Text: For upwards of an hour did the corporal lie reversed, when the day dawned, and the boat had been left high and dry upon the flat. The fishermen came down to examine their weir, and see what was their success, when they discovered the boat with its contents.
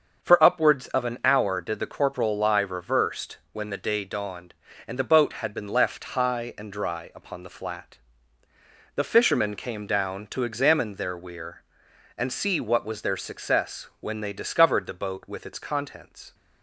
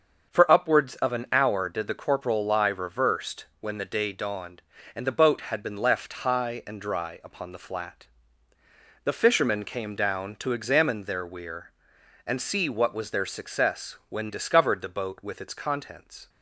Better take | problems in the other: first | starts louder than the rest; until 1.3 s; 6.5 dB; also in the first // skips "they"; at 14.2 s

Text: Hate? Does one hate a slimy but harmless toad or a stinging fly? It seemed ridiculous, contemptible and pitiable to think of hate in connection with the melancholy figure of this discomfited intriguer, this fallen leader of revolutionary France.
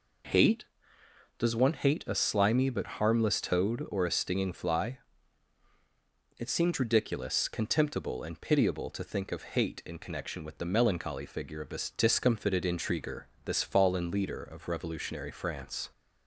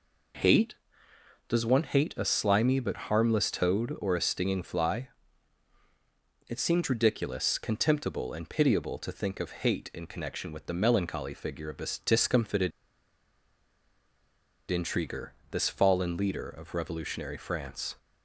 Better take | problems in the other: first | pauses between "discomfited" and "intriguer"; strong; at 12.7 s; 2.0 s long

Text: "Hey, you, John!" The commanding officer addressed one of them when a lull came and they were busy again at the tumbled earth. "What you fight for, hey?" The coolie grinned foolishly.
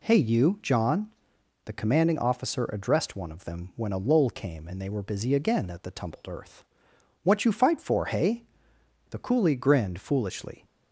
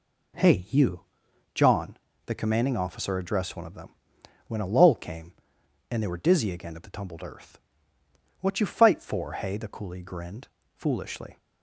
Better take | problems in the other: first | pauses between "them" and "when"; noticeable; at 3.9 s; 0.54 s long // says "dizzy" for "busy"; at 6.2 s // pauses between "grinned" and "foolishly"; slight; at 10.4 s; 0.26 s long

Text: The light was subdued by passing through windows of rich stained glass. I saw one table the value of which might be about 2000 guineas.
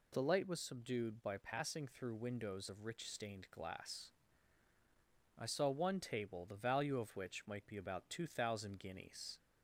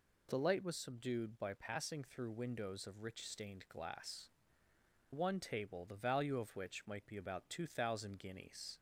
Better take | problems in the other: first | skips "I saw"; at 4.7 s

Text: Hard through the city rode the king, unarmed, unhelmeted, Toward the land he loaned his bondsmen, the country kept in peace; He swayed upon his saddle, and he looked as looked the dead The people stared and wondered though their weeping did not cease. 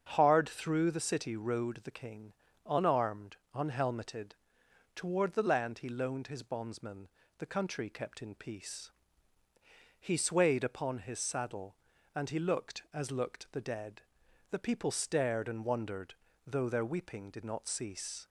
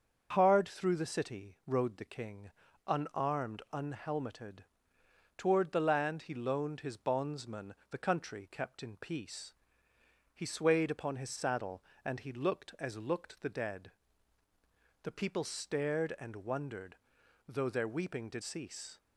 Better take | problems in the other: first | starts louder than the rest; until 1.3 s; 7 dB; strong in the first // pauses between "dead" and "The"; at 13.9 s; 1.1 s long; noticeable in the first // pauses between "wondered" and "though"; noticeable; at 16.9 s; 0.50 s long; slight in the first // skips "not"; at 18.4 s

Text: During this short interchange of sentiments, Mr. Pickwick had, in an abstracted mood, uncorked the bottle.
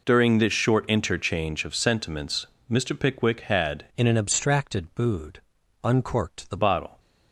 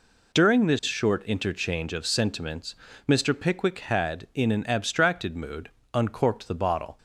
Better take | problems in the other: second | changes voice from "in" to "the"; from 3.9 to 6.5 s; 2.6 s long

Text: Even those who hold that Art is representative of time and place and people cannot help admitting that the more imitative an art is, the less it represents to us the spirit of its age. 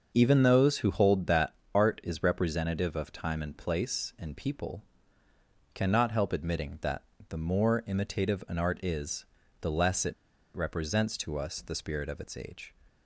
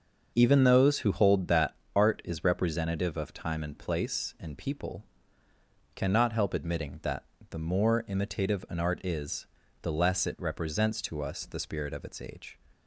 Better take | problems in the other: second | starts louder than the rest; until 1.1 s; 6.5 dB; also in the second // pauses between "that" and "Art"; slight; at 1.5 s; 0.20 s long; slight in the second // pauses between "people" and "cannot"; noticeable; at 4.8 s; 0.90 s long; noticeable in the second // pauses between "that" and "the"; slight; at 7.0 s; 0.24 s long; slight in the second // pauses between "it" and "represents"; at 10.1 s; 0.41 s long

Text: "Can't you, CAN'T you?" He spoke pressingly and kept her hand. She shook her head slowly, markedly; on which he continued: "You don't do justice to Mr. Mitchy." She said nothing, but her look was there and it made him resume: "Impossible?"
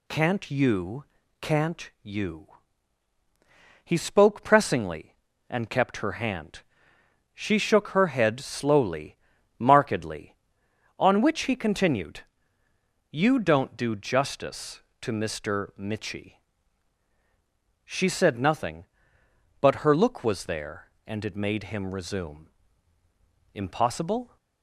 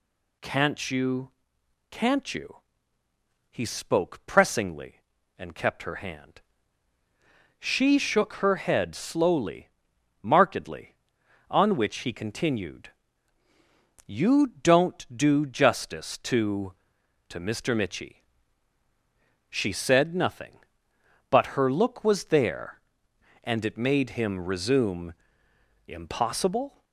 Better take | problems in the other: first | says "to" twice; at 17.2 s

